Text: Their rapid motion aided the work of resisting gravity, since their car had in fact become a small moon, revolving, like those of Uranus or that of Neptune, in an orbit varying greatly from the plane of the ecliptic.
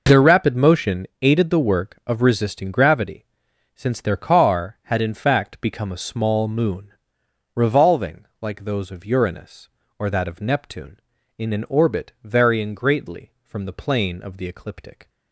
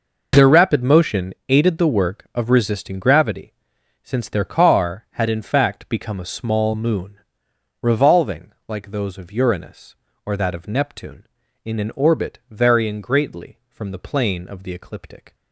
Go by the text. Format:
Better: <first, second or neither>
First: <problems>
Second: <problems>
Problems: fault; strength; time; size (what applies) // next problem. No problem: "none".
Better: neither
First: pauses between "motion" and "aided"; slight; at 1.0 s; 0.16 s long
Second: pauses between "motion" and "aided"; slight; at 1.3 s; 0.16 s long